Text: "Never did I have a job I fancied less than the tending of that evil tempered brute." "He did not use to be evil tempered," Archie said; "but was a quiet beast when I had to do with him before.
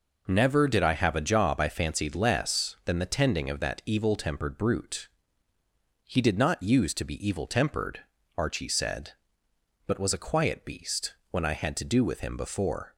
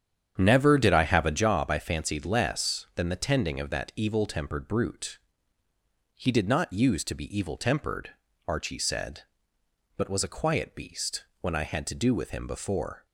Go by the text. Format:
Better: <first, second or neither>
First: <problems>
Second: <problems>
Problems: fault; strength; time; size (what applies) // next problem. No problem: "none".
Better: first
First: pauses between "beast" and "when"; slight; at 11.1 s; 0.18 s long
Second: starts louder than the rest; strong; until 1.5 s; 8.5 dB // pauses between "beast" and "when"; slight; at 11.2 s; 0.18 s long